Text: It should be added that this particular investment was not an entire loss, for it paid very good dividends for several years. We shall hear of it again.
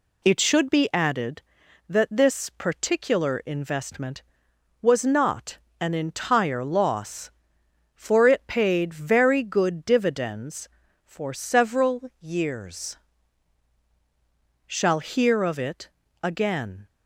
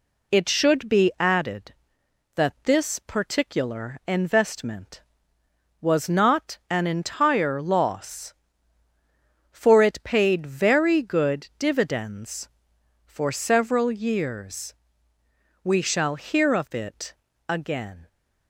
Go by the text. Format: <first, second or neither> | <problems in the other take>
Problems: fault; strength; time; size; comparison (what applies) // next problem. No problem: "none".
second | pauses between "not" and "an"; slight; at 5.5 s; 0.22 s long // skips "We"; at 13.8 s // pauses between "it" and "again"; slight; at 15.8 s; 0.34 s long; slight in the second